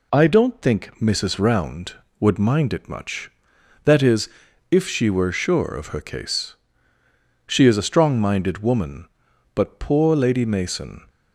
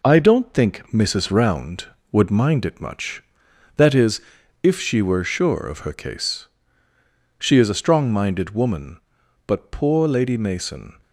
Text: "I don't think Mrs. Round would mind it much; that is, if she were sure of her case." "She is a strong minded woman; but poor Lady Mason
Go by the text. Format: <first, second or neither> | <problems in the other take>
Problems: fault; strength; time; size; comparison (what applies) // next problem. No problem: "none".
first | gets quieter; throughout; 3.5 dB